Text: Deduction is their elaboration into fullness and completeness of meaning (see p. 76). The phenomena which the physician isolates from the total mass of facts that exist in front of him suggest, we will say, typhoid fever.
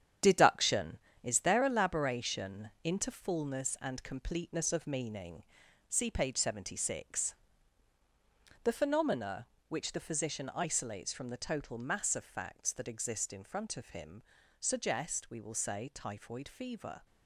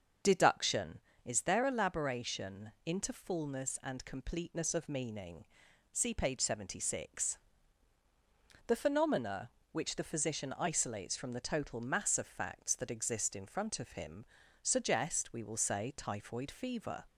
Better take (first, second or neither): second